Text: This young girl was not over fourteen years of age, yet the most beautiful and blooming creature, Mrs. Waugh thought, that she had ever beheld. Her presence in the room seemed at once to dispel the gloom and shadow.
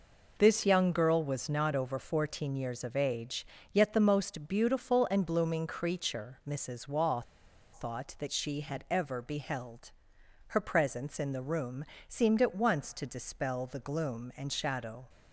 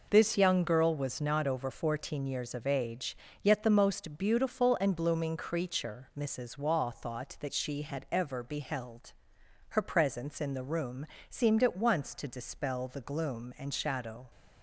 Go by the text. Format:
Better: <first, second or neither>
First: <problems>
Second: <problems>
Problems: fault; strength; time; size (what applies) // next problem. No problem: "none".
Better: second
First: pauses between "Waugh" and "thought"; noticeable; at 7.2 s; 0.50 s long // pauses between "room" and "seemed"; slight; at 11.8 s; 0.22 s long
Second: pauses between "room" and "seemed"; slight; at 11.0 s; 0.22 s long